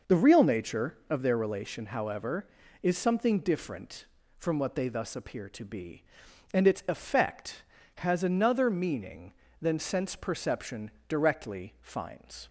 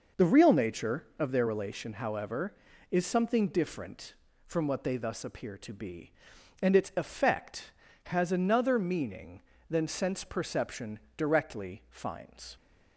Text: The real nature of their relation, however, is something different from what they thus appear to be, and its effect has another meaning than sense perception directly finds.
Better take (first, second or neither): neither